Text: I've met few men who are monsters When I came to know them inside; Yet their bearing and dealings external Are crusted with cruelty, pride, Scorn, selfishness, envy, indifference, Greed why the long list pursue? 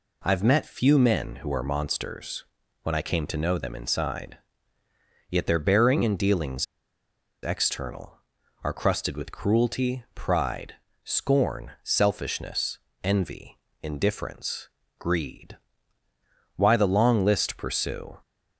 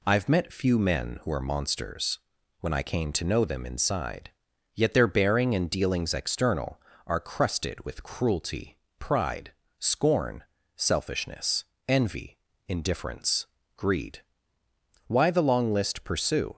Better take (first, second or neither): second